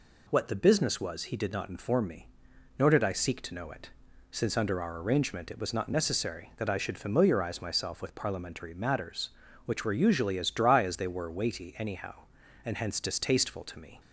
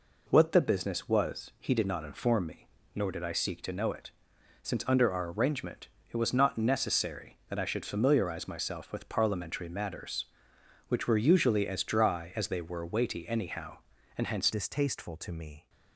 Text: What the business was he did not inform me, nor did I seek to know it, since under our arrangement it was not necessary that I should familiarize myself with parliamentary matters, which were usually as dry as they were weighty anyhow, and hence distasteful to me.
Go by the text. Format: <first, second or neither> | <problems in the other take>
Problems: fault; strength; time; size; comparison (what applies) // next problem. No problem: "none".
first | pauses between "arrangement" and "it"; slight; at 5.8 s; 0.24 s long // changes voice at "distasteful"; from 14.5 s on; 1.1 s long